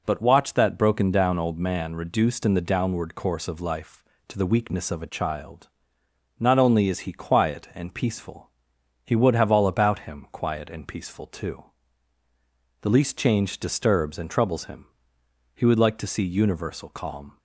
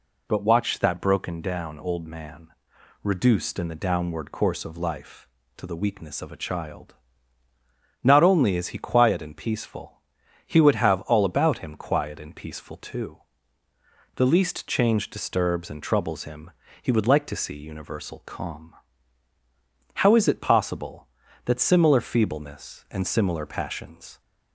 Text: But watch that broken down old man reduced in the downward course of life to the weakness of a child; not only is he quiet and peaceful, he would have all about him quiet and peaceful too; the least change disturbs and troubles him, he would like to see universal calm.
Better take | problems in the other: first | pauses between "man" and "reduced"; noticeable; at 2.4 s; 0.54 s long // goes on to say "How is it possible that similar feebleness and similar passions"; strong; from 19.9 s on; 4.2 s long

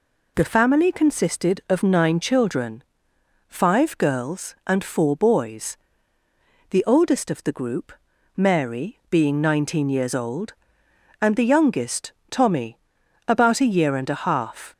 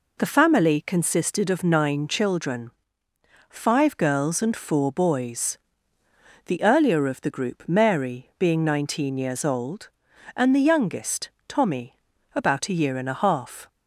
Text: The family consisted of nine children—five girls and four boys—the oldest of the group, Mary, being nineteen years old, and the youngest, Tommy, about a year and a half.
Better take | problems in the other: first | says "earlier" for "oldest"; at 6.6 s

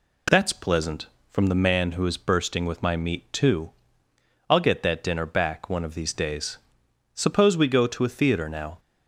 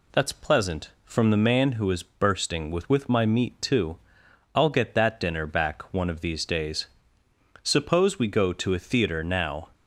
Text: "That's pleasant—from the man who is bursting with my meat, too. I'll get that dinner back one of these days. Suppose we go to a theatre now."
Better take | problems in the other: first | says "with" twice; at 2.8 s

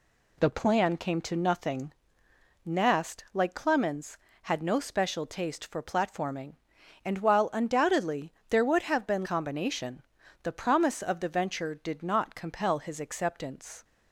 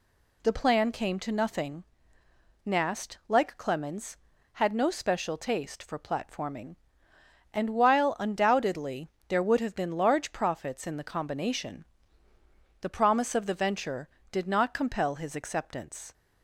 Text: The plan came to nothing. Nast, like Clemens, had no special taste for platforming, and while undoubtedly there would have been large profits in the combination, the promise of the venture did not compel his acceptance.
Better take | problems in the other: second | pauses between "undoubtedly" and "there"; slight; at 8.3 s; 0.18 s long; slight in the second // skips "large profits in the"; at 9.2 s

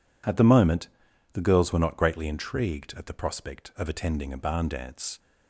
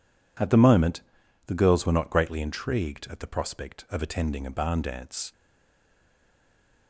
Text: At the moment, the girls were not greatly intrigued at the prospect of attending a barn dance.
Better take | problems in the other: first | stays silent after the last word; noticeable; from 5.3 s on; 1.5 s long

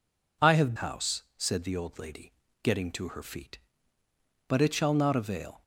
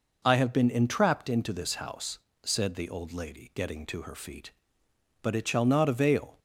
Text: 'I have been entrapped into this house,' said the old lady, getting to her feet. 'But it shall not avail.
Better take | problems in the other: second | skips "been entrapped into this"; at 0.7 s

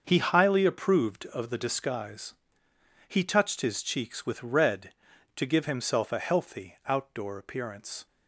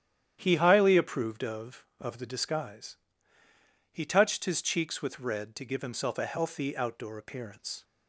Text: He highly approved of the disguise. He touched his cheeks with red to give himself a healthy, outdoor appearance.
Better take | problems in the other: first | starts louder than the rest; strong; until 1.4 s; 10 dB; also in the first // says "of" twice; at 1.9 s

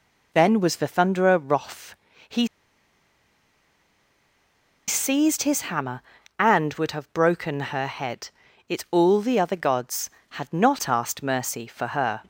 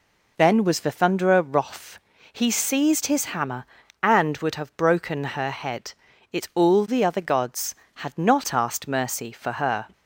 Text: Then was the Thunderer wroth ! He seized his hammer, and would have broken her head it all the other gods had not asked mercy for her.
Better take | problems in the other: second | pauses between "He" and "seized"; strong; at 2.4 s; 2.4 s long // pauses between "head" and "it"; at 8.2 s; 0.38 s long; also in the second

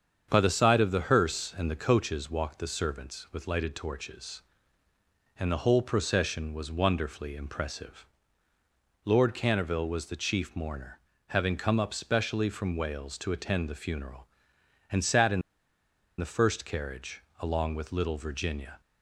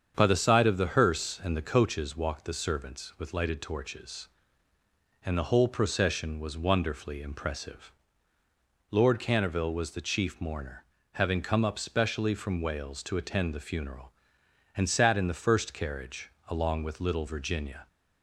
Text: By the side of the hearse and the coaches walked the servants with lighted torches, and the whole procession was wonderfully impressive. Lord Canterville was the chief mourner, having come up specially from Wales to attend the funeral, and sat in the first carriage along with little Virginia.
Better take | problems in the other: second | starts louder than the rest; strong; until 1.3 s; 7.5 dB; strong in the second // pauses between "in" and "the"; noticeable; at 15.4 s; 0.76 s long // pauses between "carriage" and "along"; slight; at 17.2 s; 0.16 s long; slight in the second

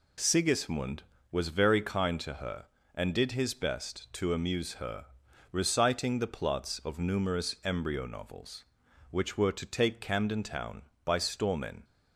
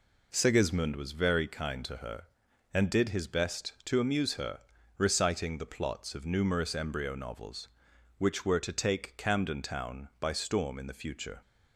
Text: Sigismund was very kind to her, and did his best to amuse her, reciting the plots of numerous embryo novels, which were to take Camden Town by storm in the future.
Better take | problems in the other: second | stops before "the future"; at 11.8 s

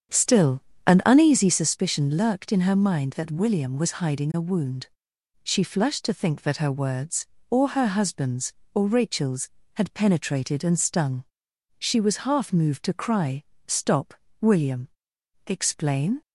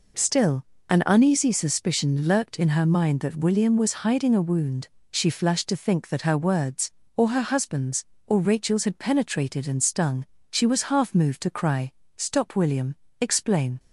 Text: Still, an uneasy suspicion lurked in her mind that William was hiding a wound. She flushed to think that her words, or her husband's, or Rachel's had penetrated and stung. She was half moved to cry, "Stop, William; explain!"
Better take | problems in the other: second | starts louder than the rest; strong; until 1.6 s; 8 dB

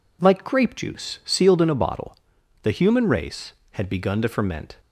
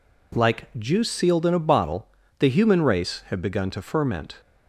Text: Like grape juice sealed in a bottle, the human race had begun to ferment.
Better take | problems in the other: first | skips "grape"; at 0.7 s

